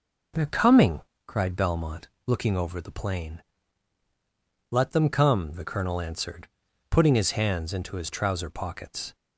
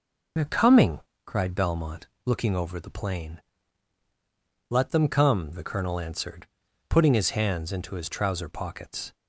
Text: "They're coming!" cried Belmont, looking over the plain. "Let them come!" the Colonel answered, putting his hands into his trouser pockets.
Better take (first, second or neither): first